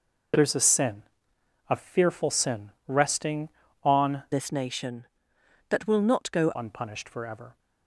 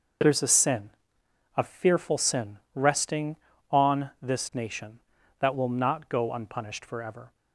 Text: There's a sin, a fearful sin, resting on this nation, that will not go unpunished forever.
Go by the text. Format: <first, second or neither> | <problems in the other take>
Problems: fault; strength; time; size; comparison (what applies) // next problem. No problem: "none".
second | changes voice from "this" to "go"; from 4.3 to 6.5 s; 2.2 s long